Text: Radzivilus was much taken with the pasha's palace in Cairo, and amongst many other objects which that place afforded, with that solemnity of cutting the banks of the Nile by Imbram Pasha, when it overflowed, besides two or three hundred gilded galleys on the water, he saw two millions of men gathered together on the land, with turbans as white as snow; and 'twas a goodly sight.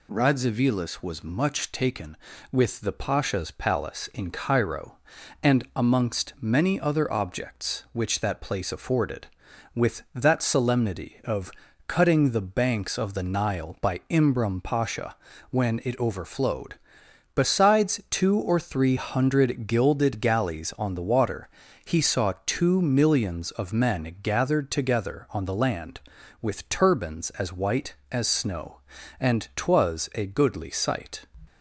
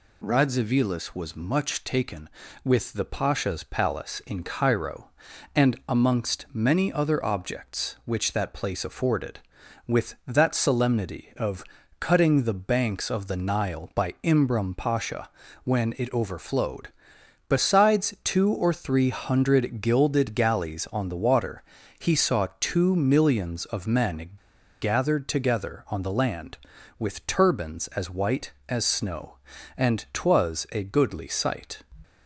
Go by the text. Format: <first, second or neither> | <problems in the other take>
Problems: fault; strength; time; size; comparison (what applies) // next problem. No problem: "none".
first | pauses between "of" and "cutting"; slight; at 11.6 s; 0.34 s long; slight in the first // pauses between "men" and "gathered"; noticeable; at 24.2 s; 0.53 s long